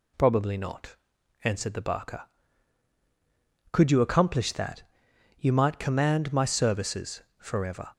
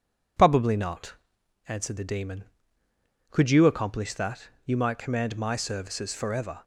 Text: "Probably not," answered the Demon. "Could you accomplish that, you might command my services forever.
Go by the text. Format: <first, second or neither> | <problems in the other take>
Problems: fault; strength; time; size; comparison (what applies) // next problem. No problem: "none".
second | says "Barker" for "Demon"; at 1.8 s // pauses between "services" and "forever"; slight; at 7.2 s; 0.15 s long